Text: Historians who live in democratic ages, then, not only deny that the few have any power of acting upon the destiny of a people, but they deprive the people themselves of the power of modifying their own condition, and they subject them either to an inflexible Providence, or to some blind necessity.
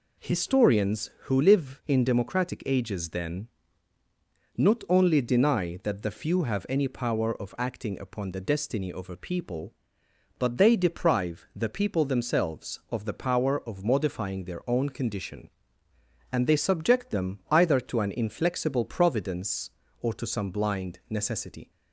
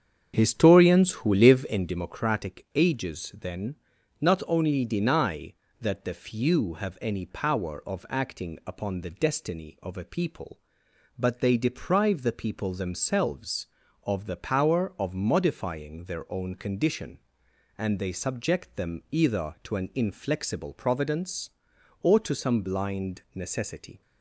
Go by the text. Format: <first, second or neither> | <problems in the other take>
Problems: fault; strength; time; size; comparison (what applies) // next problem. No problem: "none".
first | starts louder than the rest; strong; until 2.1 s; 7.5 dB